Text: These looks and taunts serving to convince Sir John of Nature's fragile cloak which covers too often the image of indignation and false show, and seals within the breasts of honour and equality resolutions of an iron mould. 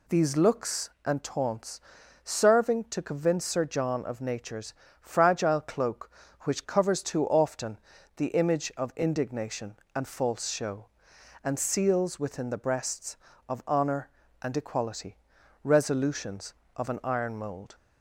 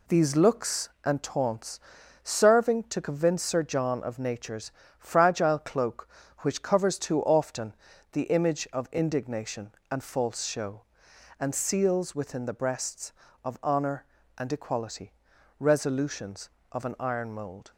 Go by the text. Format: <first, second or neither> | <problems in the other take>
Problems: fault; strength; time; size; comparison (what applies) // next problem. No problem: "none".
first | gets quieter; noticeable; throughout; 5.5 dB // pauses between "taunts" and "serving"; at 1.7 s; 0.42 s long; also in the first // pauses between "Nature's" and "fragile"; slight; at 4.7 s; 0.28 s long; slight in the first // pauses between "often" and "the"; at 7.7 s; 0.40 s long; also in the first // pauses between "equality" and "resolutions"; noticeable; at 15.1 s; 0.46 s long; noticeable in the first